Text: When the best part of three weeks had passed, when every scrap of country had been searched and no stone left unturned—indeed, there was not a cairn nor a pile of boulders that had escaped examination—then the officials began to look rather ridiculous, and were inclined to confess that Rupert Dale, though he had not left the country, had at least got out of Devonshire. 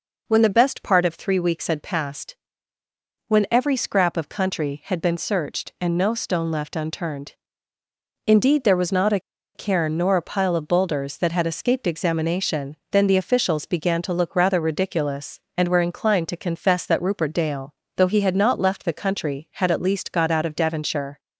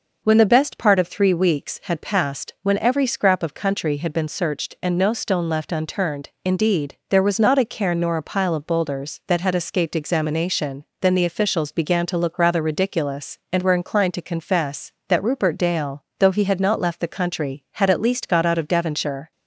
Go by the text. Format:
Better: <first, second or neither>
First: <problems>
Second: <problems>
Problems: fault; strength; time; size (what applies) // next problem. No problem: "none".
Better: second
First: pauses between "a" and "cairn"; slight; at 9.1 s; 0.35 s long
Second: none